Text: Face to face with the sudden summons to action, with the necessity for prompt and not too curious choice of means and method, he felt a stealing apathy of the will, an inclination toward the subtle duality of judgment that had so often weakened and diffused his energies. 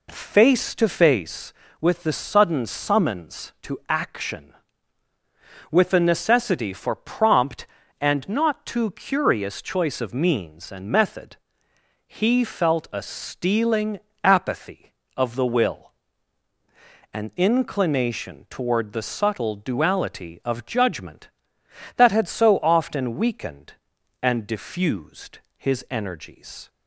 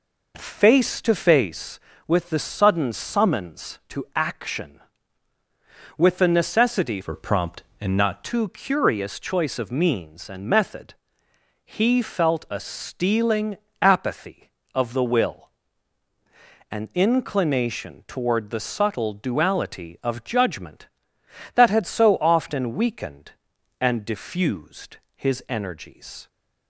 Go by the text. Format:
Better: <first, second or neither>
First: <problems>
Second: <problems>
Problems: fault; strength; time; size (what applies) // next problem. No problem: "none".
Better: first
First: pauses between "stealing" and "apathy"; slight; at 13.9 s; 0.26 s long // pauses between "diffused" and "his"; slight; at 25.3 s; 0.18 s long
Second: changes voice from "for" to "not"; from 7.0 to 8.2 s; 1.2 s long // pauses between "stealing" and "apathy"; slight; at 13.5 s; 0.26 s long // pauses between "diffused" and "his"; slight; at 24.9 s; 0.18 s long